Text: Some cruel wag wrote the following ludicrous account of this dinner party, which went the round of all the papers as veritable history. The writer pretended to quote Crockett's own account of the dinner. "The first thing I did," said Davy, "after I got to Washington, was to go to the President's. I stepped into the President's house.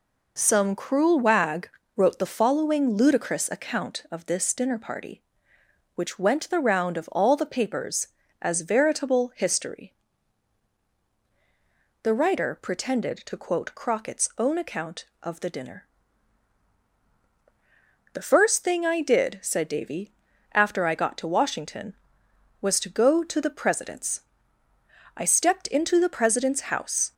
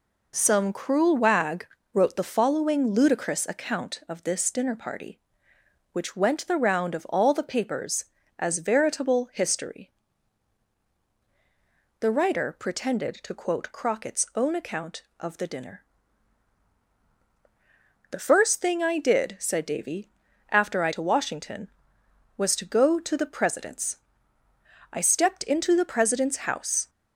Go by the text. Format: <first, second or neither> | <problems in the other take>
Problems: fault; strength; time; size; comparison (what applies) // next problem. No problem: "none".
first | pauses between "wag" and "wrote"; slight; at 1.6 s; 0.28 s long; slight in the first // skips "got"; at 20.9 s